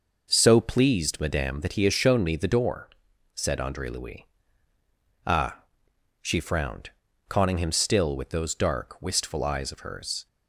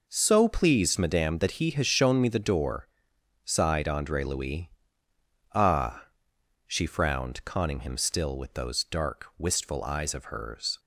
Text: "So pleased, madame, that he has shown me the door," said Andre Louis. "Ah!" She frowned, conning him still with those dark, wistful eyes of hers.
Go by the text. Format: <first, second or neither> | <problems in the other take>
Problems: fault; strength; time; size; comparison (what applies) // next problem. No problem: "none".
first | says "sighed" for "said"; at 3.4 s